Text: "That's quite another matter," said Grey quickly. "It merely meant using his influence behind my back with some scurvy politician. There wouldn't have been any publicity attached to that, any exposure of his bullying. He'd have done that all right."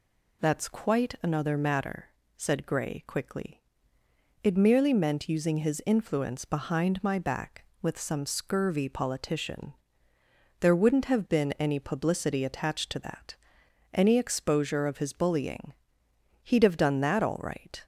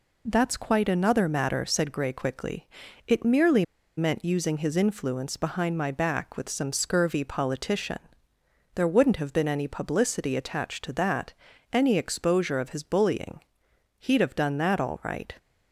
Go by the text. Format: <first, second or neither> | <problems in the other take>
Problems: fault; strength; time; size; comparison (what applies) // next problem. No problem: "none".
first | pauses between "merely" and "meant"; slight; at 3.6 s; 0.33 s long